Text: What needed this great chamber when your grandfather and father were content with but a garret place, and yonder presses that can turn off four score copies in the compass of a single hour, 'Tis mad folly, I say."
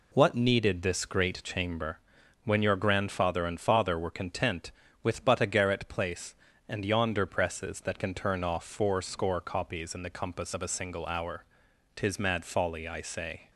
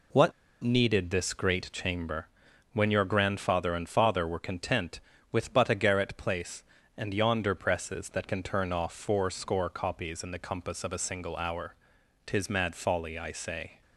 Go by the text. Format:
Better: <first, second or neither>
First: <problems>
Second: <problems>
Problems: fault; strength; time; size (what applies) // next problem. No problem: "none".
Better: first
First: pauses between "chamber" and "when"; noticeable; at 1.9 s; 0.46 s long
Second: pauses between "What" and "needed"; slight; at 0.3 s; 0.31 s long // pauses between "chamber" and "when"; noticeable; at 2.2 s; 0.46 s long